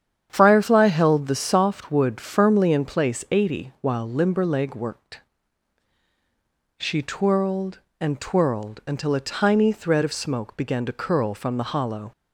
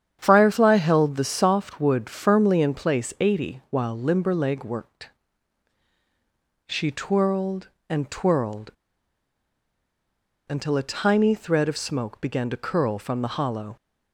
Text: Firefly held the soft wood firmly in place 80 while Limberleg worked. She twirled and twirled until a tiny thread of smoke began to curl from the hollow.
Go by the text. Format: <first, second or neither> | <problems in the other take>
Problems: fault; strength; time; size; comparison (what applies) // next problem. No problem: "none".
first | starts louder than the rest; strong; until 1.2 s; 8.5 dB; strong in the first // pauses between "twirled" and "until"; strong; at 8.6 s; 1.7 s long